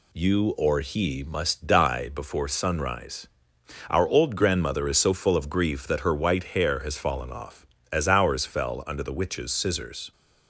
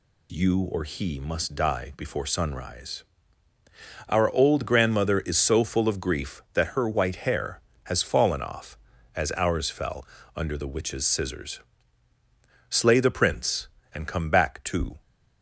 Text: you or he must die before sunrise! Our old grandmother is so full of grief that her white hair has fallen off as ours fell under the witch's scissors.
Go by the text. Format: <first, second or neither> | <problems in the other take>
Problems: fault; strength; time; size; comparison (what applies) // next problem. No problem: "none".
first | pauses between "fell" and "under"; slight; at 10.0 s; 0.30 s long // goes on to say "Slay the prince and come back to"; strong; from 12.6 s on; 2.3 s long